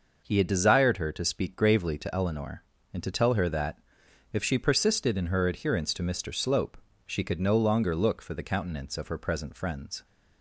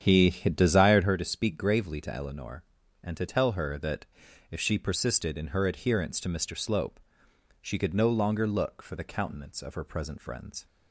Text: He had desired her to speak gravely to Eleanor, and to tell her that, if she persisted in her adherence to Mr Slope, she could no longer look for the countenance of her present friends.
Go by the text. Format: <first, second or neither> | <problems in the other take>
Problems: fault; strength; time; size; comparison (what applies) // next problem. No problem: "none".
first | starts louder than the rest; strong; until 1.1 s; 8.5 dB